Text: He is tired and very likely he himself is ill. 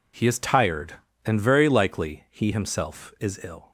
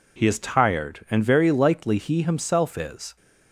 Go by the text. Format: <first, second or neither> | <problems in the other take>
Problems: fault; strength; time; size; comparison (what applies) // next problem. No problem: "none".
first | stops before "ill"; at 3.1 s